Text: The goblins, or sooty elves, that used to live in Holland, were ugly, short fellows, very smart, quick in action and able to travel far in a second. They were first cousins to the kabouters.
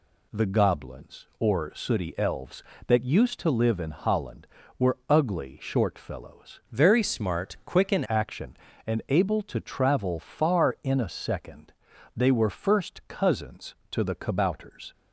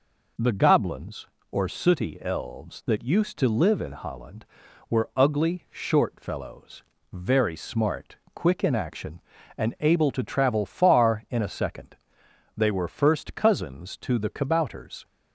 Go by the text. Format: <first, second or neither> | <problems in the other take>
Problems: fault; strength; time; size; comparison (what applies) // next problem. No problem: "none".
second | changes voice from "very" to "in"; from 6.7 to 8.0 s; 1.3 s long